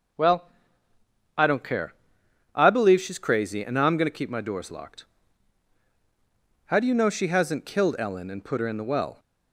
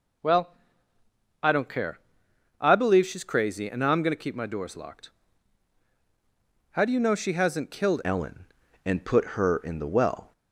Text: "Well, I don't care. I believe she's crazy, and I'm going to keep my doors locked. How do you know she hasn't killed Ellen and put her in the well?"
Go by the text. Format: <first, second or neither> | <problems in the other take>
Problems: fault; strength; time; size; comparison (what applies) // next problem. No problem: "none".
first | changes voice at "Ellen"; from 8.0 s on; 2.3 s long